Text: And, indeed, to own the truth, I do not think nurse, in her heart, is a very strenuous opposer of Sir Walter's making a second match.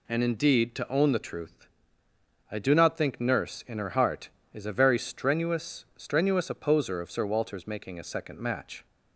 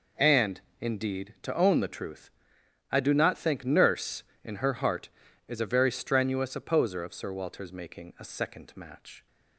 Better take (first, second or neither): second